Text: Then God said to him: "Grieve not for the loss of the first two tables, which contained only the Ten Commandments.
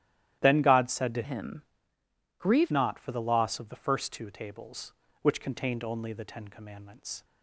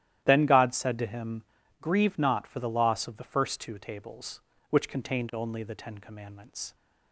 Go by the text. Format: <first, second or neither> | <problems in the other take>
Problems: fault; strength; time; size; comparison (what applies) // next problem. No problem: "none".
second | starts louder than the rest; strong; until 1.4 s; 12.5 dB; strong in the second // changes voice from "him" to "Grieve"; from 1.2 to 2.7 s; 1.5 s long